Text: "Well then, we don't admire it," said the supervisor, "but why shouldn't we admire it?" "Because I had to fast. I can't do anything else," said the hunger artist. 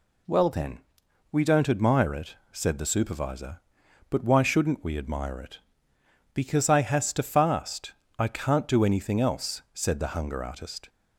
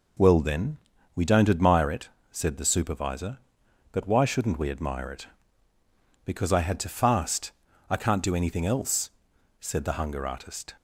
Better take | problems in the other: second | says "has" for "had"; at 6.8 s

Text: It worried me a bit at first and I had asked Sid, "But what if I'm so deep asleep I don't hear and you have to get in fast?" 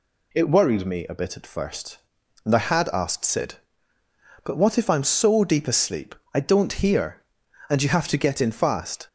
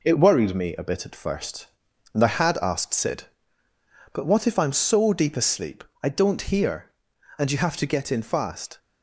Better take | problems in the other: first | gets quieter; noticeable; throughout; 4 dB // pauses between "asleep" and "I"; slight; at 5.8 s; 0.18 s long; slight in the first

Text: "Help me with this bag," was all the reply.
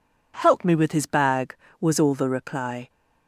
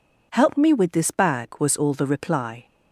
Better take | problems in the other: second | says "his" for "this"; at 0.9 s

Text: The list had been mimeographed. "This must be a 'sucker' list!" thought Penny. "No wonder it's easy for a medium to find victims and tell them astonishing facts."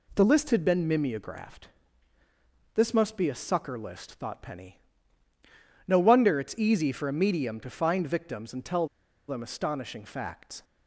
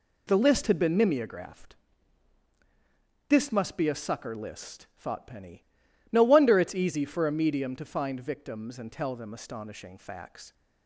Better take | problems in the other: second | pauses between "tell" and "them"; at 8.8 s; 0.40 s long

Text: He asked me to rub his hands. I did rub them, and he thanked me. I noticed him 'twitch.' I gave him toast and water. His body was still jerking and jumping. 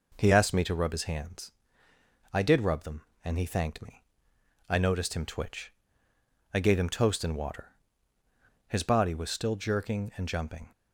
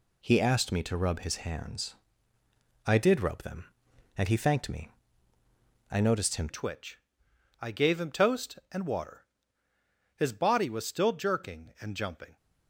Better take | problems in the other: first | changes voice at "twitch"; from 6.4 s on; 5.9 s long

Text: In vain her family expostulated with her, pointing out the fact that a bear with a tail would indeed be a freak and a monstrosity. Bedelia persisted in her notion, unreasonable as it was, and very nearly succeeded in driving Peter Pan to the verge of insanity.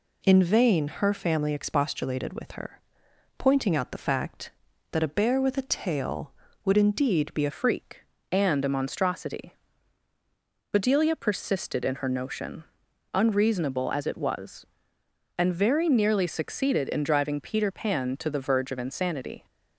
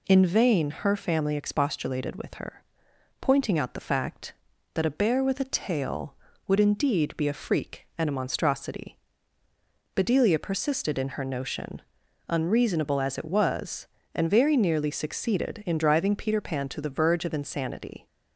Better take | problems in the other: second | changes voice at "freak"; from 7.5 s on; 11.9 s long

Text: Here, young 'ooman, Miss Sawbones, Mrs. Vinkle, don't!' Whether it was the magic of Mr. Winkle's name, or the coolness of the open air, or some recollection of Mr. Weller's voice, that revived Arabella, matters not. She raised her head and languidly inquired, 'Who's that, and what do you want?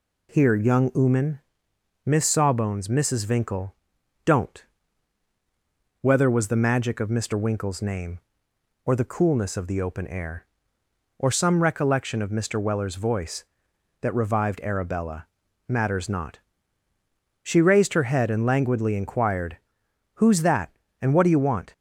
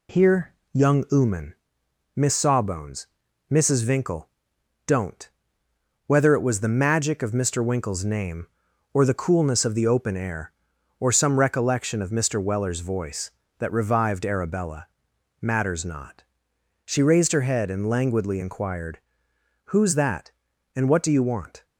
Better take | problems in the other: second | skips "it"; at 6.2 s

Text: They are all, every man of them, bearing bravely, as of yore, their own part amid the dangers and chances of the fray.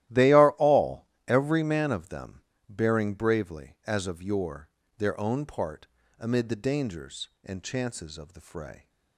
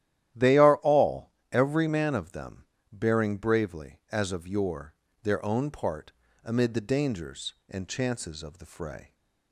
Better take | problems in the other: second | gets quieter; strong; throughout; 14.5 dB // starts louder than the rest; strong; until 1.3 s; 14 dB; strong in the second // pauses between "part" and "amid"; slight; at 5.8 s; 0.32 s long; slight in the second

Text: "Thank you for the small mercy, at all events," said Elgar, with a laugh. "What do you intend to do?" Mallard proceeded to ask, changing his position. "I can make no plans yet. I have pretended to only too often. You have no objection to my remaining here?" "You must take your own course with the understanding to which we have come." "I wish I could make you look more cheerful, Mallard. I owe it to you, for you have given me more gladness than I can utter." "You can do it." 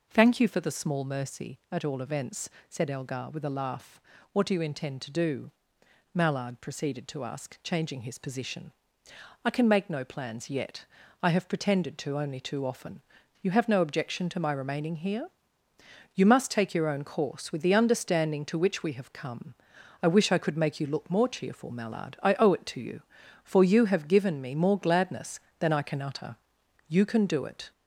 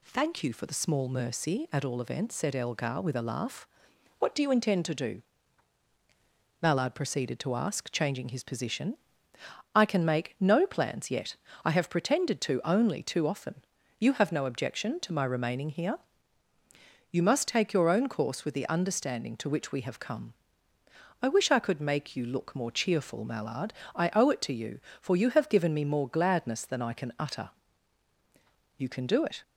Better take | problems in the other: second | gets louder; slight; throughout; 3 dB

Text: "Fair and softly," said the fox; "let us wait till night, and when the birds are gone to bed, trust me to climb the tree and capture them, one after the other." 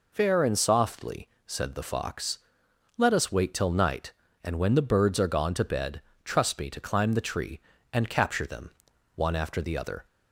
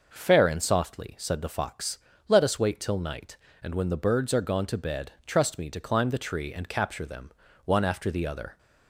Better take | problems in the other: neither | none

